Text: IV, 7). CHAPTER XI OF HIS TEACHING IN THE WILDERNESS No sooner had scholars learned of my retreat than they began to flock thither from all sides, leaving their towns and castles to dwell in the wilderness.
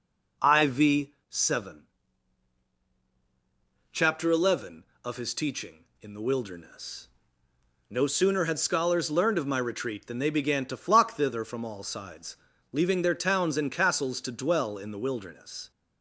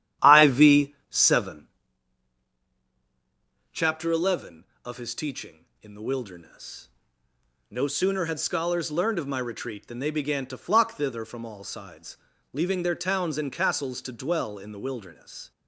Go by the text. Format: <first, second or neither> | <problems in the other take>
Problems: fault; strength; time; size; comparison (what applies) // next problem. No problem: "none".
first | starts louder than the rest; strong; until 2.0 s; 11 dB // pauses between "WILDERNESS" and "No"; noticeable; at 6.8 s; 0.82 s long; noticeable in the first